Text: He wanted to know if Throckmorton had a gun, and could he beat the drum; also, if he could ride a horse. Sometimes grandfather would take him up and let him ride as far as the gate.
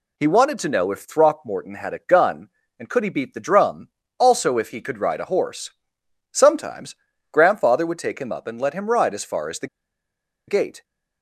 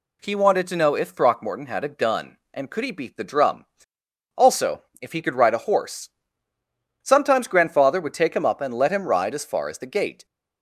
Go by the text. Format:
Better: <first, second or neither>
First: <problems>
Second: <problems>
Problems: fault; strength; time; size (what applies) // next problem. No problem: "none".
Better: second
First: pauses between "Sometimes" and "grandfather"; at 6.9 s; 0.38 s long // pauses between "the" and "gate"; noticeable; at 9.6 s; 0.81 s long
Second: none